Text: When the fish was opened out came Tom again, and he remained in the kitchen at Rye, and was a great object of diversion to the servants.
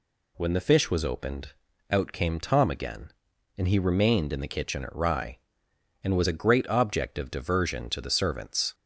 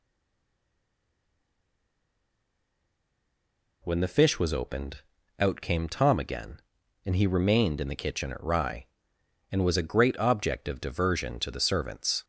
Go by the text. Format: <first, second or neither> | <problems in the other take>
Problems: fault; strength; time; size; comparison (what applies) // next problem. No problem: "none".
first | stays silent before the first word; strong; until 3.8 s; 3.8 s long // pauses between "opened" and "out"; at 5.0 s; 0.40 s long; also in the first